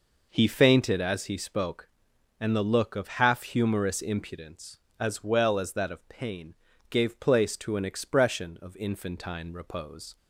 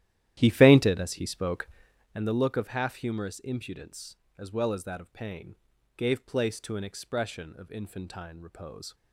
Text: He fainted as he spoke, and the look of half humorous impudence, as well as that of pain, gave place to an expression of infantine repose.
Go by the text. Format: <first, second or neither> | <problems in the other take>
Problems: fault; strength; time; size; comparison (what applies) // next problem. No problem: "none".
first | starts louder than the rest; strong; until 2.2 s; 12.5 dB